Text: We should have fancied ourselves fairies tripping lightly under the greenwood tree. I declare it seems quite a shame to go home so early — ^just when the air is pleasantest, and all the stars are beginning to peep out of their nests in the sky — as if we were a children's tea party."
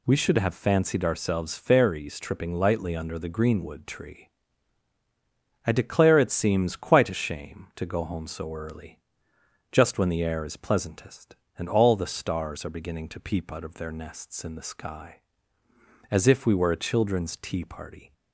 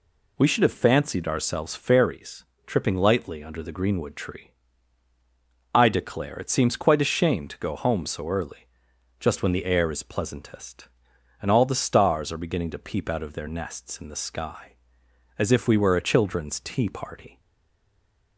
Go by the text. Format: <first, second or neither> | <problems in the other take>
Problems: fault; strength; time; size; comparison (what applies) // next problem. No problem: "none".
first | pauses between "fairies" and "tripping"; slight; at 2.4 s; 0.20 s long // stays silent after the last word; from 17.3 s on; 1.0 s long